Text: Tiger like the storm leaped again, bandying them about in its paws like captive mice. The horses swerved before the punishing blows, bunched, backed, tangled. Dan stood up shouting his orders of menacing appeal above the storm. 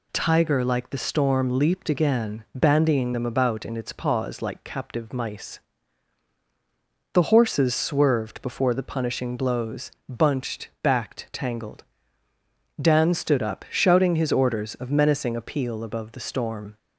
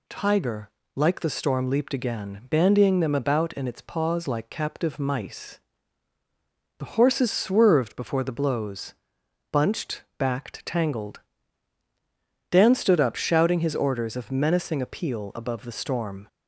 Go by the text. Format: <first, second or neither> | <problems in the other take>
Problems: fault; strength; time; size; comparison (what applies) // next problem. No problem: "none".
first | pauses between "Tiger" and "like"; slight; at 0.7 s; 0.24 s long // skips "punishing"; at 8.3 s